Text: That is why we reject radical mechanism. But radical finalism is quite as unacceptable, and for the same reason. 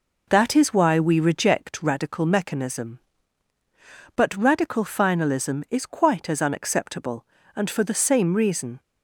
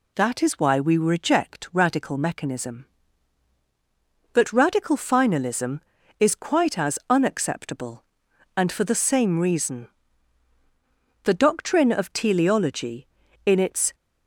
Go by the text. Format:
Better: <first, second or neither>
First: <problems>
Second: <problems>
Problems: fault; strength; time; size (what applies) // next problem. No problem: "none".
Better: first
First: none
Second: goes on to say "The doctrine of teleology in its"; strong; from 11.2 s on; 2.7 s long